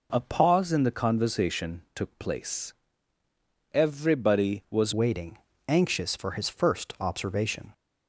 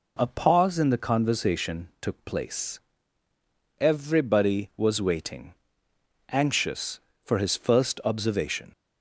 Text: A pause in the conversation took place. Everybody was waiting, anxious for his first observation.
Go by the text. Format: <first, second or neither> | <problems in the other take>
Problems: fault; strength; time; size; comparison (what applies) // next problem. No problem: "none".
second | changes voice at "waiting"; from 4.9 s on; 2.8 s long